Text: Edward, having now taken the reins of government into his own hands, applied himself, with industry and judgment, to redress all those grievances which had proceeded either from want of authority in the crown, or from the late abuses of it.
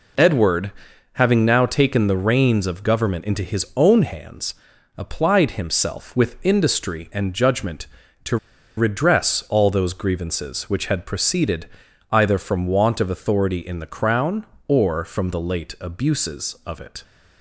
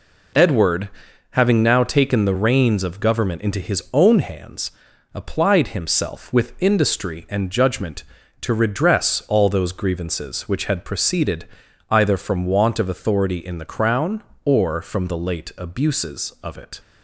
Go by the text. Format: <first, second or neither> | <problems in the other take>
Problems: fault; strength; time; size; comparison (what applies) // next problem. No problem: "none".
second | pauses between "to" and "redress"; at 8.3 s; 0.40 s long // pauses between "proceeded" and "either"; at 11.6 s; 0.44 s long; also in the second